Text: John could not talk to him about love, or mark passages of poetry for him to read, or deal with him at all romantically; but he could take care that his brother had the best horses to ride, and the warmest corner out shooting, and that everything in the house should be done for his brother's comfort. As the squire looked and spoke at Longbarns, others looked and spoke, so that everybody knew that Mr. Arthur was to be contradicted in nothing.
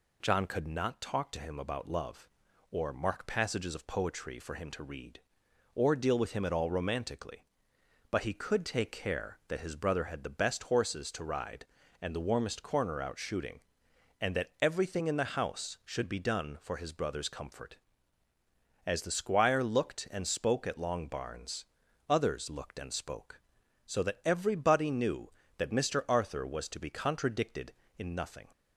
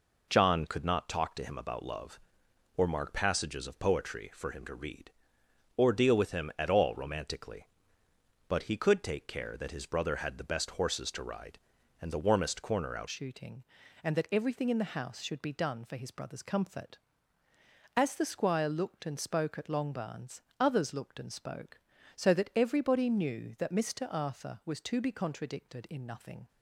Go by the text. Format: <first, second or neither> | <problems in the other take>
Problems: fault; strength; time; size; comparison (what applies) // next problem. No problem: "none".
first | changes voice at "shooting"; from 13.0 s on; 13.4 s long